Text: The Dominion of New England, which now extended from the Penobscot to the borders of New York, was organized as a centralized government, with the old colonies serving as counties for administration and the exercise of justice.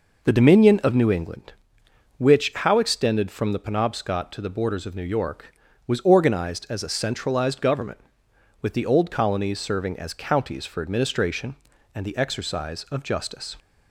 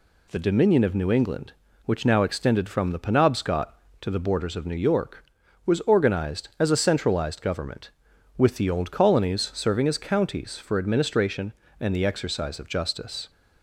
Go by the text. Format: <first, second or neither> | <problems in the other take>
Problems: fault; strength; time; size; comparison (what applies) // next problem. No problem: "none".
second | says "how" for "now"; at 2.5 s